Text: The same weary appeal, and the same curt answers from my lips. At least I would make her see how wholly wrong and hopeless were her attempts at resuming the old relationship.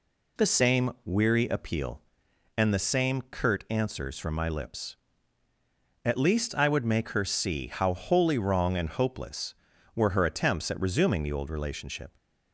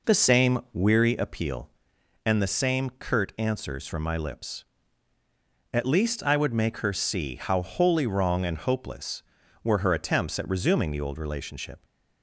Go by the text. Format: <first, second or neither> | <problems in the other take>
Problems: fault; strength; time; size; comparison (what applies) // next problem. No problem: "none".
first | starts louder than the rest; noticeable; until 1.1 s; 4.5 dB